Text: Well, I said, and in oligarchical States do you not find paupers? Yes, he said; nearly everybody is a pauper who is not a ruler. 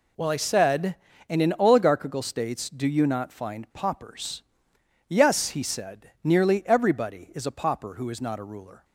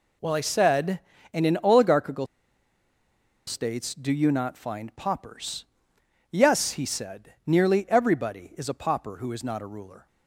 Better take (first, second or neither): first